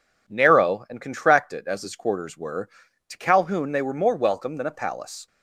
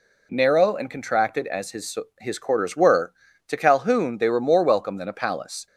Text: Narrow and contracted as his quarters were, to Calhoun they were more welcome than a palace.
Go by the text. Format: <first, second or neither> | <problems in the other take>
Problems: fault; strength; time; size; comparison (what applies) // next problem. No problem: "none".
first | says "his" twice; at 2.2 s